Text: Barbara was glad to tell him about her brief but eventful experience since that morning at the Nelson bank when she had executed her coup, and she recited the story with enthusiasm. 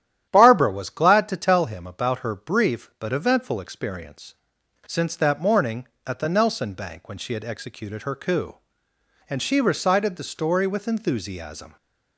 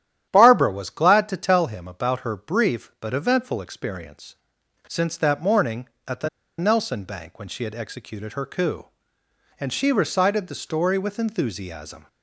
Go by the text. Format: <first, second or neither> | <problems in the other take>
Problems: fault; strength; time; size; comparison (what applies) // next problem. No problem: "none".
first | starts louder than the rest; strong; until 1.3 s; 11 dB; strong in the first // pauses between "experience" and "since"; noticeable; at 4.3 s; 0.54 s long; noticeable in the first // pauses between "the" and "Nelson"; slight; at 6.2 s; 0.30 s long